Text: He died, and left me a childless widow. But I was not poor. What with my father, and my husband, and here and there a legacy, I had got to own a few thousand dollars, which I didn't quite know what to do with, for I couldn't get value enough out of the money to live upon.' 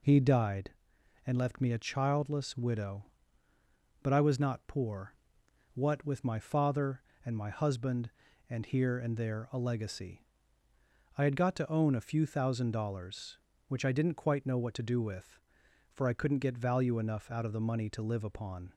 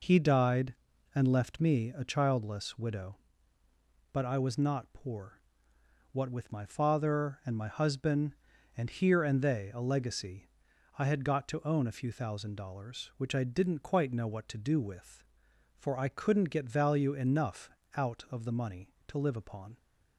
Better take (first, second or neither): first